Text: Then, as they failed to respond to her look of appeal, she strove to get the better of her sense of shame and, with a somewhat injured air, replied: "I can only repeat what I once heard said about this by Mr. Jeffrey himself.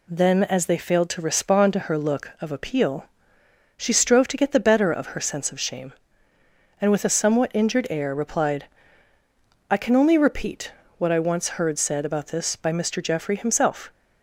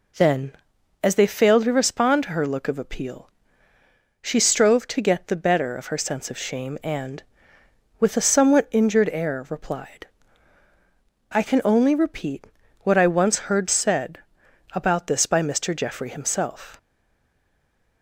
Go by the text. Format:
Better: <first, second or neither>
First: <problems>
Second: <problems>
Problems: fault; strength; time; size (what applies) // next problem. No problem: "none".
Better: first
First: pauses between "repeat" and "what"; slight; at 10.7 s; 0.26 s long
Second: pauses between "repeat" and "what"; at 12.4 s; 0.38 s long // pauses between "said" and "about"; noticeable; at 14.1 s; 0.56 s long // stays silent after the last word; noticeable; from 16.7 s on; 1.3 s long